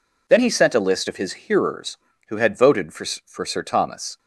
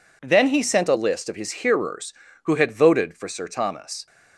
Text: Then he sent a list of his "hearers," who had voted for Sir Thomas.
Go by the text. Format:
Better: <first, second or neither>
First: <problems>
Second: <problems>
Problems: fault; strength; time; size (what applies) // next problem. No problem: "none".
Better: second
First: says "for" twice; at 3.2 s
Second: none